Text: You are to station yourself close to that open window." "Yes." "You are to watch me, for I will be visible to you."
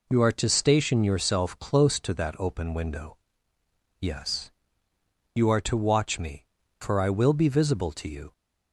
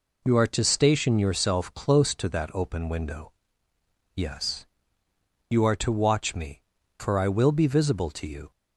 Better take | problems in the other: neither | none

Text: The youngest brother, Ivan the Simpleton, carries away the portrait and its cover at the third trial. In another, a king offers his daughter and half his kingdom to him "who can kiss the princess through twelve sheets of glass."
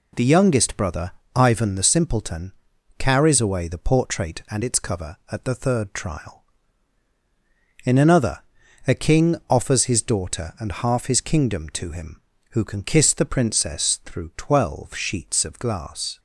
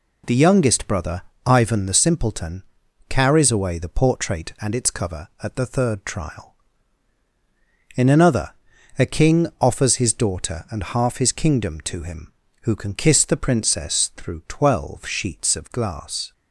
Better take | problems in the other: neither | none

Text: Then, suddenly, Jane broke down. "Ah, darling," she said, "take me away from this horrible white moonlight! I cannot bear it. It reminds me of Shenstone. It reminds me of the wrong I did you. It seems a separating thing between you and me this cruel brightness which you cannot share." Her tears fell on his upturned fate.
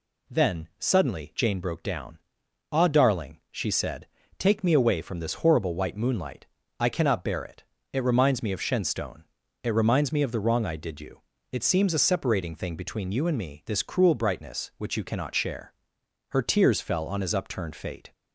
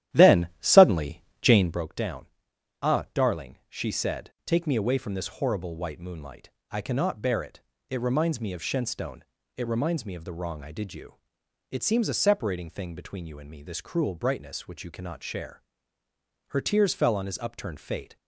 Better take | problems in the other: first | starts louder than the rest; strong; until 1.9 s; 12.5 dB

